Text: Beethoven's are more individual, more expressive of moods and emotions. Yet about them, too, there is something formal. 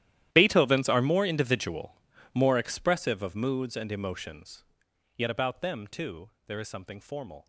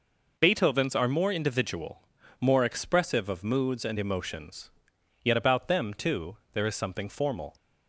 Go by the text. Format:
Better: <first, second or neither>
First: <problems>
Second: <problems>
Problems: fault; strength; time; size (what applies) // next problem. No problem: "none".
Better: second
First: gets quieter; strong; throughout; 18.5 dB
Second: none